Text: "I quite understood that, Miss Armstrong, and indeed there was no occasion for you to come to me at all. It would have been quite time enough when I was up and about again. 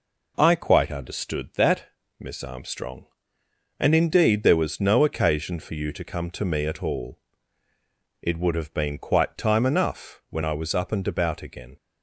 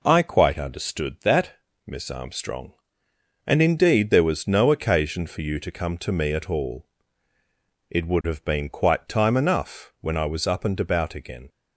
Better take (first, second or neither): neither